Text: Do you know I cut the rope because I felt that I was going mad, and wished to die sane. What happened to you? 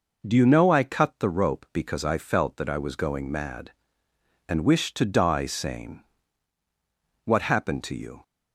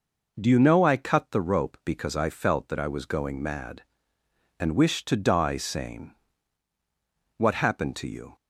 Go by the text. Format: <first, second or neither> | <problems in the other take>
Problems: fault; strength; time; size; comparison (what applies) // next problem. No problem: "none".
neither | none